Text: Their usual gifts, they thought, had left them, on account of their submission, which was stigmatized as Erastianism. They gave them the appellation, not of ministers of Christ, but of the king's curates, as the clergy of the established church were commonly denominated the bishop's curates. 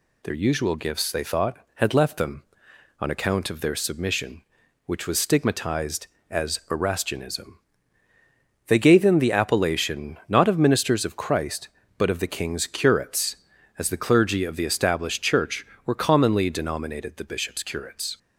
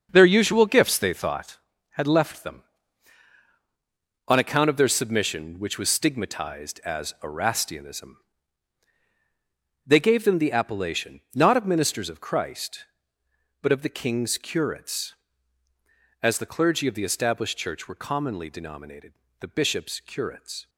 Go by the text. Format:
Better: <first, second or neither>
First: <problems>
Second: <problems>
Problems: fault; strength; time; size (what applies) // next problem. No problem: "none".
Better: first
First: none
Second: starts louder than the rest; until 1.6 s; 6.5 dB // pauses between "denominated" and "the"; slight; at 19.1 s; 0.28 s long